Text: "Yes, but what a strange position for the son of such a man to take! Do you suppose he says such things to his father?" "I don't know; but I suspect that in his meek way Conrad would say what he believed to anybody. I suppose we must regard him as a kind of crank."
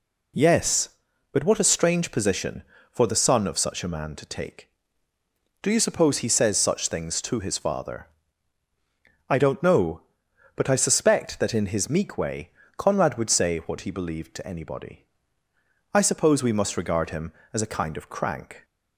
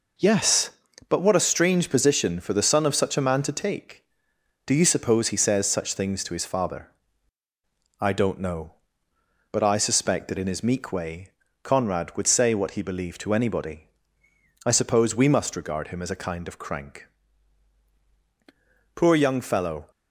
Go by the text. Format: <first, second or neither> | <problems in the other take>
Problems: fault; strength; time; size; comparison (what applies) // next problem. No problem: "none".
first | pauses between "way" and "Conrad"; slight; at 11.3 s; 0.30 s long; slight in the first // goes on to say "Poor young fellow"; noticeable; from 18.9 s on; 0.96 s long